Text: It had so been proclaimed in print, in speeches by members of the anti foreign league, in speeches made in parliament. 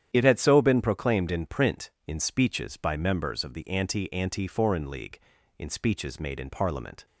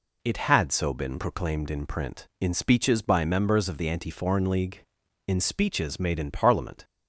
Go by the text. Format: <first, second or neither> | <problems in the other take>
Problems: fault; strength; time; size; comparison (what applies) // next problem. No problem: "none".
second | starts louder than the rest; strong; until 1.1 s; 9.5 dB // says "anti" twice; at 4.1 s